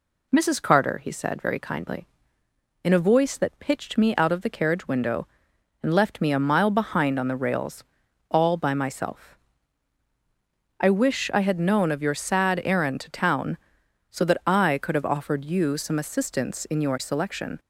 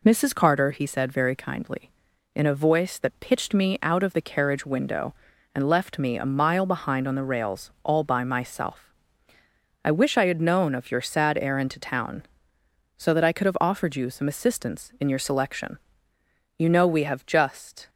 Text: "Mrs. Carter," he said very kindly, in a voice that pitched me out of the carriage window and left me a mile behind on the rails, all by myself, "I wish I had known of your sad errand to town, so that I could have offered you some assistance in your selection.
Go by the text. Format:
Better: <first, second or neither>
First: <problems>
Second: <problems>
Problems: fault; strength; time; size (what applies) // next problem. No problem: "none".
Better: first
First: none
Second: goes on to say "You know we have just"; from 16.5 s on; 1.3 s long